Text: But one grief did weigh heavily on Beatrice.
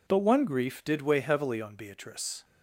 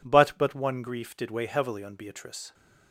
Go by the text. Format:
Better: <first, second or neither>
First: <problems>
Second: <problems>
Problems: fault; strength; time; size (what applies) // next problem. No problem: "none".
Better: first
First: none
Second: says "But" twice; at 0.3 s